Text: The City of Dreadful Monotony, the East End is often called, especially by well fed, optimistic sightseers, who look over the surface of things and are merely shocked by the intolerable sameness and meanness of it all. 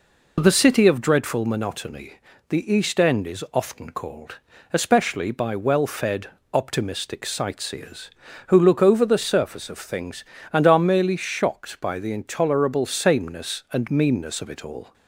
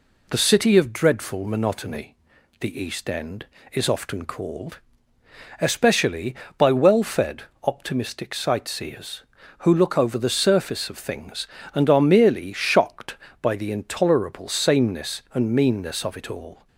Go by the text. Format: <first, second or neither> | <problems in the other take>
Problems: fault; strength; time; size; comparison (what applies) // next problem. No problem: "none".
neither | none